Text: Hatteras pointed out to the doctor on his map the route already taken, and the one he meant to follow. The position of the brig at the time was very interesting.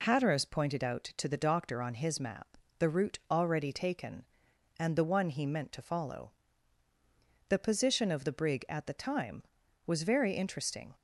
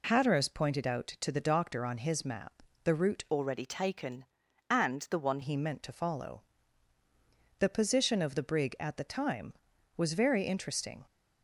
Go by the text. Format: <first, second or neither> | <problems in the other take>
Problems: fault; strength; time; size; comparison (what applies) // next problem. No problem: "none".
first | pauses between "map" and "the"; slight; at 2.6 s; 0.22 s long; slight in the first // changes voice from "already" to "one"; from 3.3 to 5.3 s; 2.0 s long